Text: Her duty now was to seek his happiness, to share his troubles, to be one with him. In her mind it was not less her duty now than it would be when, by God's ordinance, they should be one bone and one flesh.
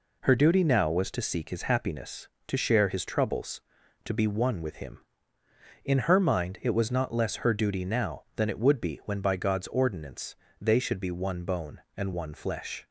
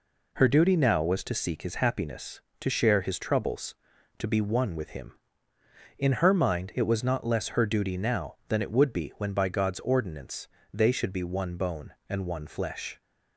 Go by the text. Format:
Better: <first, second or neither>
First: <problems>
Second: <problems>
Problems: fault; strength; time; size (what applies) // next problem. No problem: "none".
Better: neither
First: none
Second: none